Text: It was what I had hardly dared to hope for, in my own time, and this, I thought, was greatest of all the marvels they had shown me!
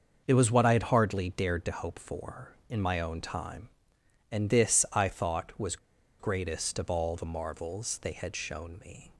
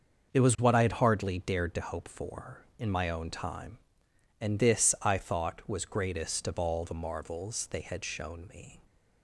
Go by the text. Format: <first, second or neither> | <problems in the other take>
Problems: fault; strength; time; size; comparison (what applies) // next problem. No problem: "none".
second | starts louder than the rest; until 1.2 s; 6.5 dB; also in the second // pauses between "was" and "greatest"; at 5.7 s; 0.43 s long